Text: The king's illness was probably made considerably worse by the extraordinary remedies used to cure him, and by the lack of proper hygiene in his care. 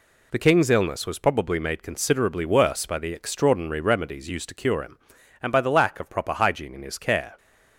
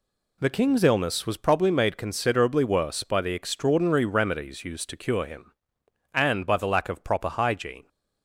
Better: first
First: none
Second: stops before "in his care"; at 7.8 s

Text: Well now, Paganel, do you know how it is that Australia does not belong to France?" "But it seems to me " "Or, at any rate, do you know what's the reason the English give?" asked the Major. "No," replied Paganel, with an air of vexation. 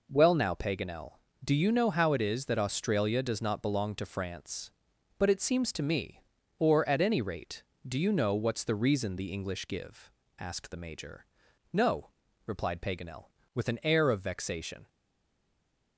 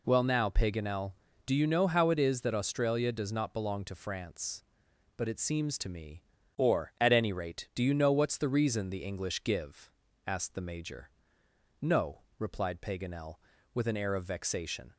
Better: second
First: stays silent after the last word; from 14.8 s on; 1.1 s long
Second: none

